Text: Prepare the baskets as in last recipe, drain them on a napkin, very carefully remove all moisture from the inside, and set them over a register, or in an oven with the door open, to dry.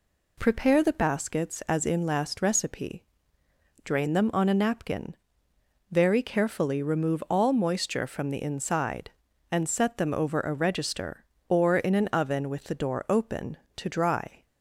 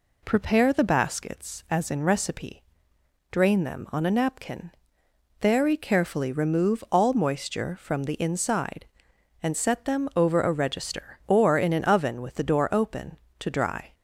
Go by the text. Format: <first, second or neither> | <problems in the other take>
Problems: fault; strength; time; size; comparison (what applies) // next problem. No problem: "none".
first | skips "last"; at 2.0 s